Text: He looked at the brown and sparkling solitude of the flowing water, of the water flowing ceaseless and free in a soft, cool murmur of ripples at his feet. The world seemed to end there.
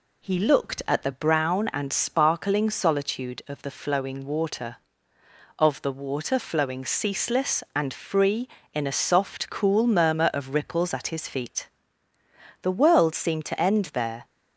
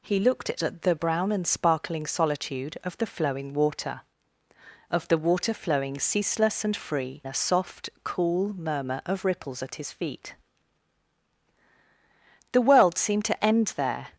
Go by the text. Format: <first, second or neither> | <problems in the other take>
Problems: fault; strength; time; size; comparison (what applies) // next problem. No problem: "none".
first | skips "in"; at 7.2 s